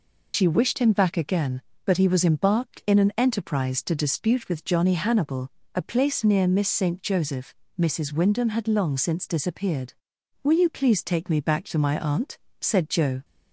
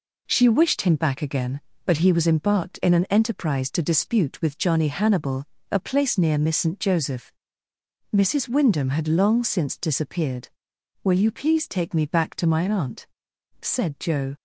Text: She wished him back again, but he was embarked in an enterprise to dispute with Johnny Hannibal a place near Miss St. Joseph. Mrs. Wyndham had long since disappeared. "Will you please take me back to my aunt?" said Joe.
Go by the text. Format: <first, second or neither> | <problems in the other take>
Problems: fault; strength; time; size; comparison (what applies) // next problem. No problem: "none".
second | loses the start of "She"; at 0.3 s; 75 ms // pauses between "Hannibal" and "a"; slight; at 5.5 s; 0.26 s long; slight in the second